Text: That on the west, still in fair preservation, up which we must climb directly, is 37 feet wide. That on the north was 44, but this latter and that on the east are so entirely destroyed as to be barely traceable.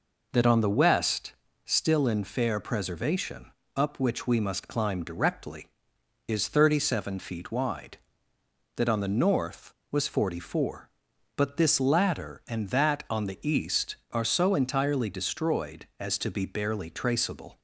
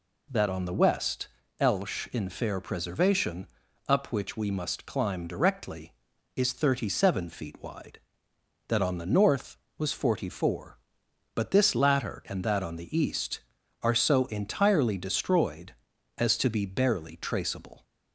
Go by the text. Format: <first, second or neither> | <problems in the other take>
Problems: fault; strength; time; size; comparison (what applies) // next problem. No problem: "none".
first | says "elsh" for "still"; at 1.5 s